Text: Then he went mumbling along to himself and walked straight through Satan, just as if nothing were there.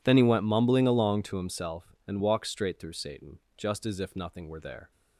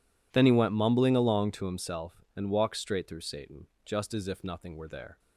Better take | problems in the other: neither | none

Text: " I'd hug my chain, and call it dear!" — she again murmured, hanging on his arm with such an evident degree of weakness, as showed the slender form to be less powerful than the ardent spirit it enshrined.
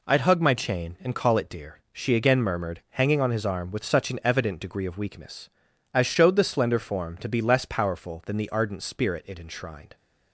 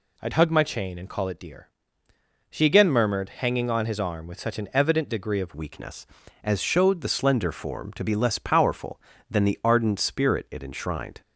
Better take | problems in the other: first | changes voice at "weakness"; from 5.5 s on; 5.7 s long

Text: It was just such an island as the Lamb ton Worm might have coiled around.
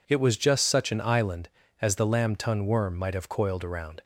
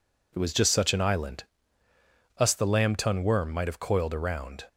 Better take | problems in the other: first | says "us" for "as"; at 2.3 s

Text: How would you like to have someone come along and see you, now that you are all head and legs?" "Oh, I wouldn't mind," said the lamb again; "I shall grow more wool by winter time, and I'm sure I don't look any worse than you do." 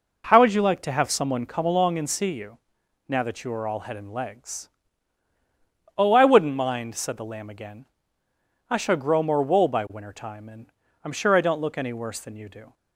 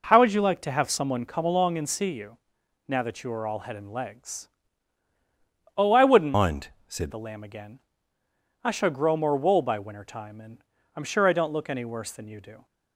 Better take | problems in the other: first | changes voice from "mind" to "said"; from 6.3 to 7.1 s; 0.8 s long // pauses between "and" and "I'm"; slight; at 10.6 s; 0.32 s long; slight in the first

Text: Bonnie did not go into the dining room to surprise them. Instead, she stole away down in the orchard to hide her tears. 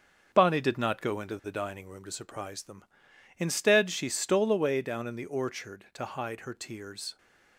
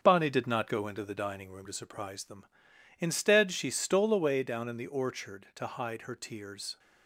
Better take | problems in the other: neither | starts louder than the rest; the same in both

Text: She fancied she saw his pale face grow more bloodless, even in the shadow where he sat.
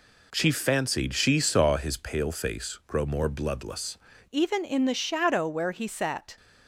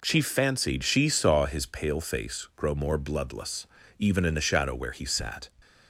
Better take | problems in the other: second | changes voice at "even"; from 4.3 s on; 2.0 s long

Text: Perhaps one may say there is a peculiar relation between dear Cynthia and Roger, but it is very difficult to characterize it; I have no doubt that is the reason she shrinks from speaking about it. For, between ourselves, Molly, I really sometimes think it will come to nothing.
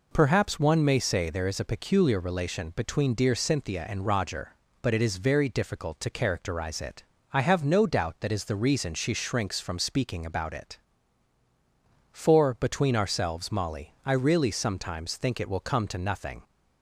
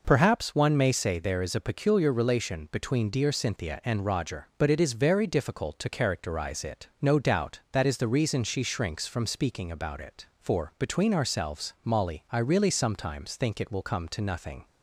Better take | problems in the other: first | skips "I have"; at 6.9 s

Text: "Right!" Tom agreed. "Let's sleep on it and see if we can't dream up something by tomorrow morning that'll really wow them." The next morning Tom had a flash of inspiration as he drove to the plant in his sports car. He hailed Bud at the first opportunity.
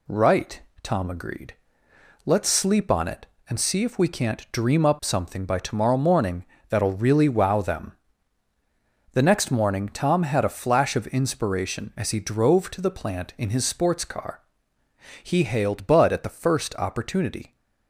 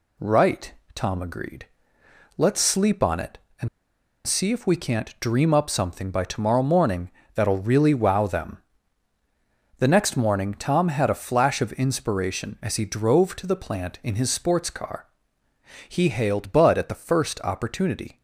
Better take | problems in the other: first | pauses between "and" and "see"; noticeable; at 3.6 s; 0.56 s long // pauses between "morning" and "that'll"; slight; at 7.1 s; 0.24 s long; slight in the first

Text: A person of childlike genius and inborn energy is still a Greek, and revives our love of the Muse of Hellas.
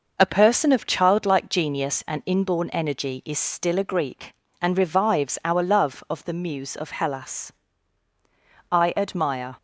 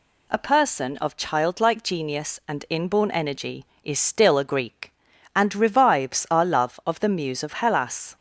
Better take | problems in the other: second | goes on to say "I admire"; noticeable; from 8.7 s on; 0.86 s long

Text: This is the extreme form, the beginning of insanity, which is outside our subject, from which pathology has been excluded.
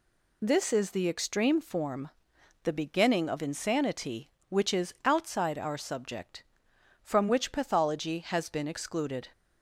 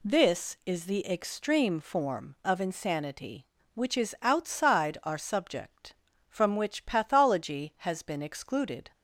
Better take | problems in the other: first | skips "the beginning"; at 2.3 s

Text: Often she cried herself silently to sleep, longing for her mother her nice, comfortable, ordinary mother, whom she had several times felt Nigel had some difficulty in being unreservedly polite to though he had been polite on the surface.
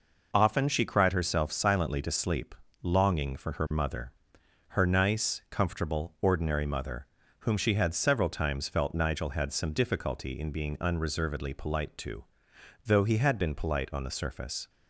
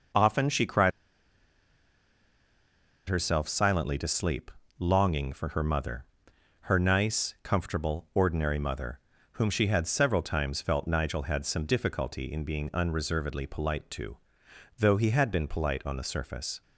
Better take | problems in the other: first | pauses between "cried" and "herself"; strong; at 0.9 s; 2.1 s long // pauses between "mother" and "her"; noticeable; at 6.0 s; 0.62 s long; noticeable in the first // pauses between "to" and "though"; noticeable; at 14.1 s; 0.62 s long; noticeable in the first

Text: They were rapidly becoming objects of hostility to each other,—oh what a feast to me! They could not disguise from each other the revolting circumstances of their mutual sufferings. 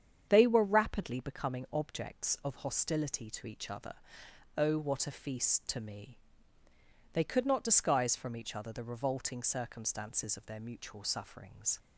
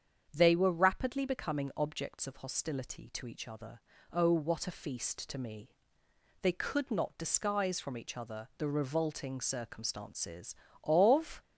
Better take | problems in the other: first | starts louder than the rest; strong; until 1.3 s; 7.5 dB; strong in the first // stops before "their mutual sufferings"; at 11.4 s

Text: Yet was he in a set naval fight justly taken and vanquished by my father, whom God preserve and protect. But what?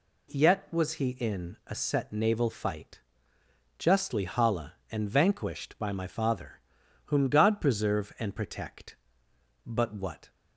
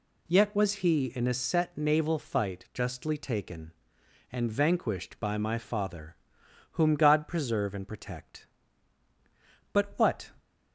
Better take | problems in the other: second | pauses between "fight" and "justly"; noticeable; at 2.9 s; 0.78 s long // says "hala" for "taken"; at 4.2 s

